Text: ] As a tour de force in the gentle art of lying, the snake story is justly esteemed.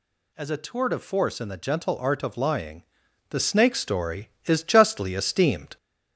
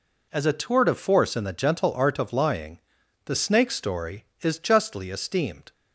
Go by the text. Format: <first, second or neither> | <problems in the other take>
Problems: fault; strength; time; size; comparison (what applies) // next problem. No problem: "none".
second | gets louder; slight; throughout; 2 dB